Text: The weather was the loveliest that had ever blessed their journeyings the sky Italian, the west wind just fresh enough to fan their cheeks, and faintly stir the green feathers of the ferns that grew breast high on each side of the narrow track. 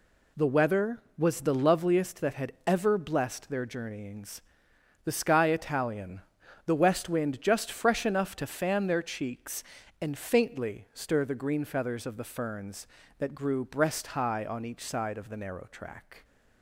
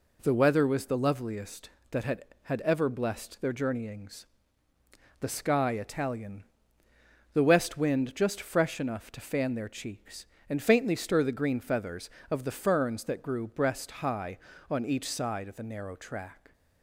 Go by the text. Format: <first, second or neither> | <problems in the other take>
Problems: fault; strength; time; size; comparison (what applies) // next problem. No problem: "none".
first | says "had" twice; at 2.4 s // pauses between "journeyings" and "the"; noticeable; at 4.2 s; 0.94 s long; noticeable in the first